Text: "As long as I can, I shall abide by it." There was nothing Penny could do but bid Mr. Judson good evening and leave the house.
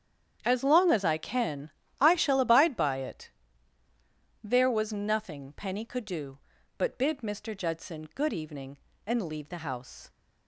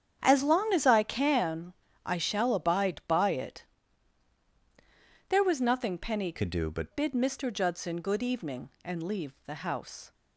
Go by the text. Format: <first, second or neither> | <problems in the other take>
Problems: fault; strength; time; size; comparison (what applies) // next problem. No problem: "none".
first | starts louder than the rest; strong; until 1.2 s; 8.5 dB; strong in the first // changes voice from "could" to "but"; from 6.3 to 6.9 s; 0.6 s long